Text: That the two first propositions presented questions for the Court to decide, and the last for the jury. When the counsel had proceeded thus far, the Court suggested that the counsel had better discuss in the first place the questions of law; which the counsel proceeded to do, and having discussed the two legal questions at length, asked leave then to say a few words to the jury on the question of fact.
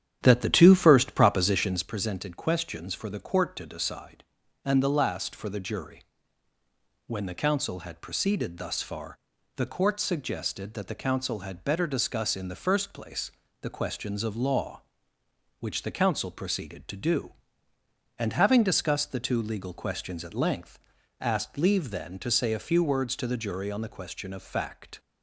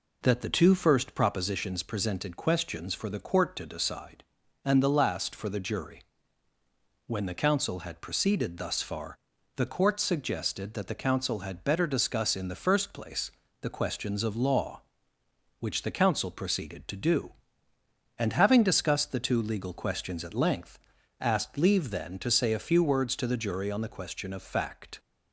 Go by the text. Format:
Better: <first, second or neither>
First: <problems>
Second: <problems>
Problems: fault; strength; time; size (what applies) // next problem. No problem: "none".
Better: second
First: starts louder than the rest; strong; until 2.0 s; 10 dB // pauses between "place" and "the"; slight; at 13.3 s; 0.30 s long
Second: pauses between "place" and "the"; slight; at 13.3 s; 0.30 s long